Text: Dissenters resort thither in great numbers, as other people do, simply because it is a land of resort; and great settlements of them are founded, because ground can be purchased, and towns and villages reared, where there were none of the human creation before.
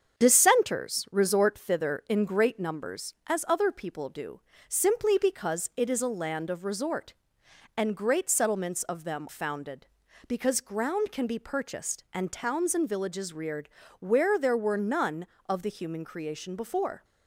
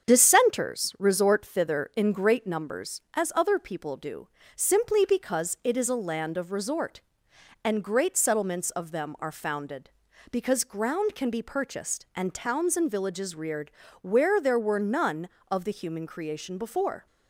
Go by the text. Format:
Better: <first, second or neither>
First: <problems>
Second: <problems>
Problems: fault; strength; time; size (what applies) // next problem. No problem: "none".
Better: second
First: starts louder than the rest; strong; until 1.2 s; 7.5 dB // skips "are"; at 9.2 s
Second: starts louder than the rest; strong; until 1.1 s; 7.5 dB